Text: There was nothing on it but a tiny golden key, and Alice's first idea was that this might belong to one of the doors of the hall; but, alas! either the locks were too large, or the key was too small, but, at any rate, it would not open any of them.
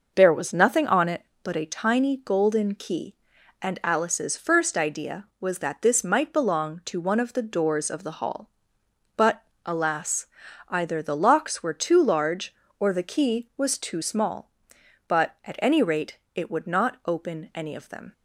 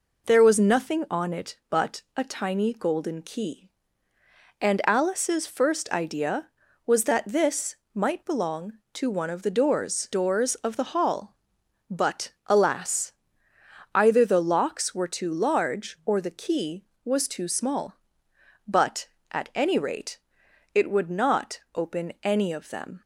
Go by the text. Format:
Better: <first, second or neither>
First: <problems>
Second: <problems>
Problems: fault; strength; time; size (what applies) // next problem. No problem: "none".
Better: first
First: none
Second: pauses between "but" and "a"; slight; at 2.0 s; 0.16 s long // pauses between "this" and "might"; slight; at 7.7 s; 0.18 s long // says "doors" twice; at 10.1 s